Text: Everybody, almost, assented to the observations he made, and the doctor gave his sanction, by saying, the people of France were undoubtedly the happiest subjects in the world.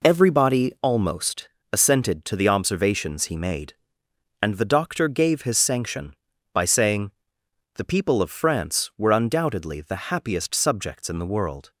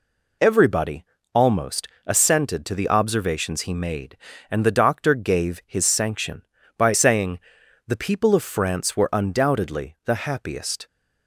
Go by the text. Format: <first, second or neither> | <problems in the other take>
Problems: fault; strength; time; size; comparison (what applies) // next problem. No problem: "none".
first | stops before "subjects in the world"; at 10.8 s